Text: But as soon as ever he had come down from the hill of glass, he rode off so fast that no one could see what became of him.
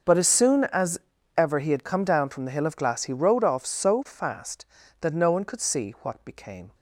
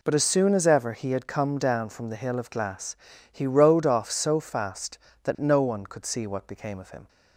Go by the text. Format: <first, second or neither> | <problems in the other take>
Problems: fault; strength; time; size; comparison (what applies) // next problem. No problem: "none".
second | starts louder than the rest; until 1.4 s; 6 dB // pauses between "as" and "ever"; at 0.9 s; 0.38 s long // stops before "of him"; at 6.7 s